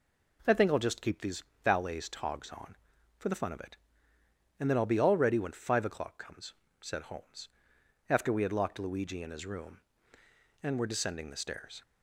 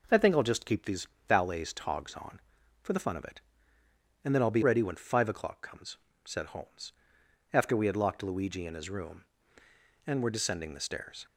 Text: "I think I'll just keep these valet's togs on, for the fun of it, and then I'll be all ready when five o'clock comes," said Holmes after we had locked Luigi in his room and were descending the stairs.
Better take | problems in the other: first | pauses between "these" and "valet's"; slight; at 1.0 s; 0.22 s long; slight in the first // skips "all"; at 4.6 s // pauses between "Holmes" and "after"; noticeable; at 6.9 s; 0.60 s long; noticeable in the first

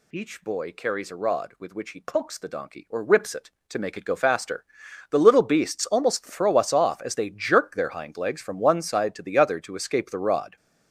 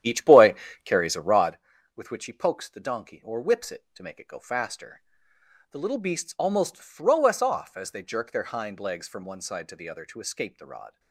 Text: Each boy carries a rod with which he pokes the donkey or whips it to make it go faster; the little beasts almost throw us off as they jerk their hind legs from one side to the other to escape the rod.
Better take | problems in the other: first | starts louder than the rest; strong; until 1.6 s; 10.5 dB // pauses between "boy" and "carries"; slight; at 0.5 s; 0.30 s long

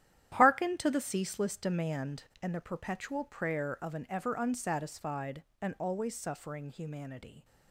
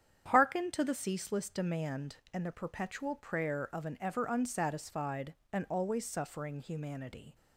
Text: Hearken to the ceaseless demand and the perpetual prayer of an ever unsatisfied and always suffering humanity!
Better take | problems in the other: second | gets quieter; strong; throughout; 11 dB // starts louder than the rest; strong; until 1.3 s; 11 dB; strong in the second

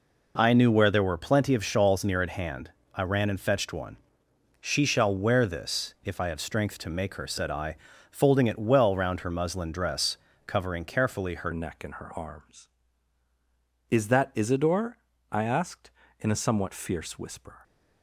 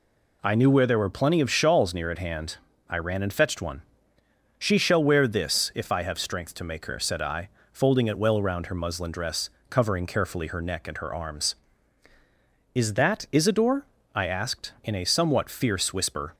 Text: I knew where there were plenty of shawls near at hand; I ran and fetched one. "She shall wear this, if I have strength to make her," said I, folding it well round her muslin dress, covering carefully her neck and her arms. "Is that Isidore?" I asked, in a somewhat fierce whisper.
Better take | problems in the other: second | changes voice at "neck"; from 11.5 s on; 6.1 s long

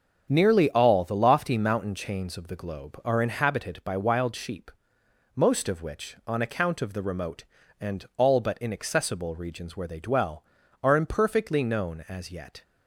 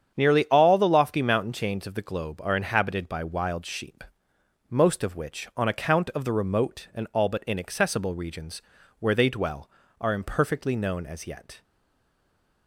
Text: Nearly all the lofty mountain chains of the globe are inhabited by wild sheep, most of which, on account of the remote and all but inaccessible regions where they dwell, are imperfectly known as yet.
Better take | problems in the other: first | starts louder than the rest; strong; until 1.2 s; 8 dB; strong in the first // pauses between "regions" and "where"; at 8.6 s; 0.38 s long // stays silent after the last word; from 11.6 s on; 1.0 s long

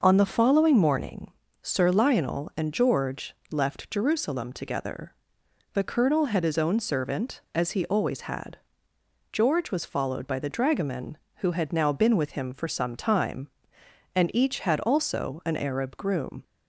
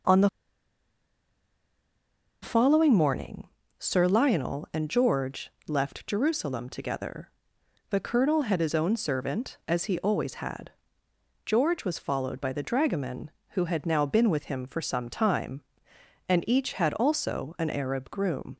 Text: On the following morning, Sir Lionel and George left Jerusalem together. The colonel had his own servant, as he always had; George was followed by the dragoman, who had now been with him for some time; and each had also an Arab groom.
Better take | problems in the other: first | pauses between "the" and "following"; strong; at 0.2 s; 2.1 s long // pauses between "George" and "left"; slight; at 5.5 s; 0.16 s long; slight in the first

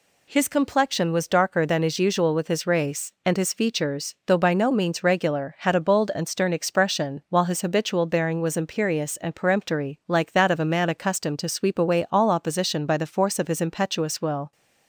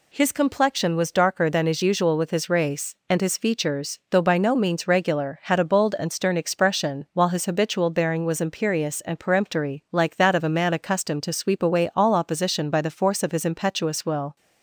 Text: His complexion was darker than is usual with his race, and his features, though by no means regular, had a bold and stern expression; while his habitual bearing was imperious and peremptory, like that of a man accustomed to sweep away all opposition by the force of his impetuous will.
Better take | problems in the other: neither | none

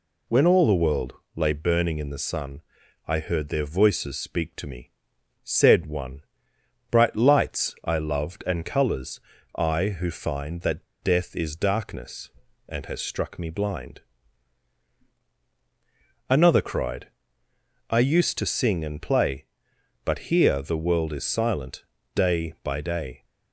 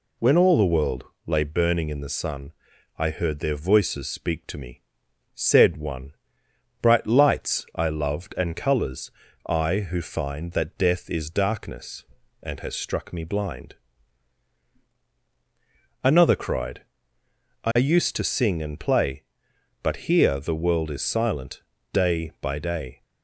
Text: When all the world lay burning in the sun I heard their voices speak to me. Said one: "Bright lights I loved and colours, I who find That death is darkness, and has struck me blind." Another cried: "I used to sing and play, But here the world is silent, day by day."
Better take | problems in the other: second | pauses between "world" and "lay"; slight; at 1.1 s; 0.22 s long; slight in the second // pauses between "sun" and "I"; noticeable; at 2.6 s; 0.46 s long; noticeable in the second // pauses between "That" and "death"; slight; at 10.8 s; 0.16 s long

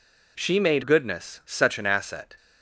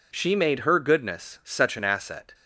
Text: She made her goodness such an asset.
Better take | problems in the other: second | skips "her"; at 0.8 s

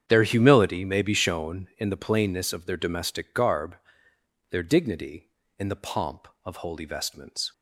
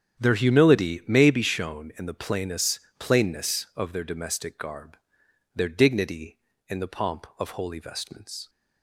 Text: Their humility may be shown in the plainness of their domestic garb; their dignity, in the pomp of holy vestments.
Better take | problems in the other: first | starts louder than the rest; strong; until 1.2 s; 8.5 dB; strong in the first // says "plainness" twice; at 2.9 s

